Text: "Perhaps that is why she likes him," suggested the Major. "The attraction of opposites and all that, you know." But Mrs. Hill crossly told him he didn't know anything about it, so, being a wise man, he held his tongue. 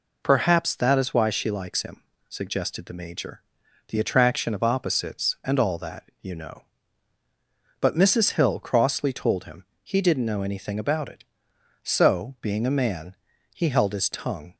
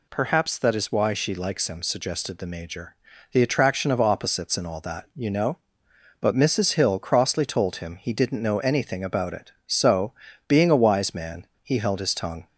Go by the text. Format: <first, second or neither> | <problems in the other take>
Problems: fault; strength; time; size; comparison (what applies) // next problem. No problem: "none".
second | pauses between "him" and "he"; slight; at 9.6 s; 0.18 s long // skips "wise"; at 12.7 s